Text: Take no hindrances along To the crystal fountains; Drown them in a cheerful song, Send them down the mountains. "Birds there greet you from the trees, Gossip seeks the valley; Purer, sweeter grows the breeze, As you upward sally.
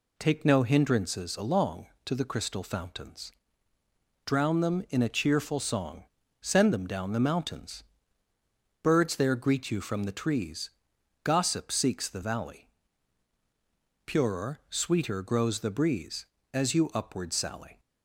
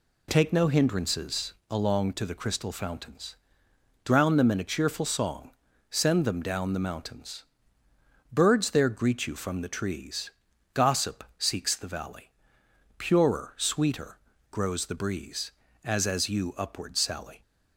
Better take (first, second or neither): first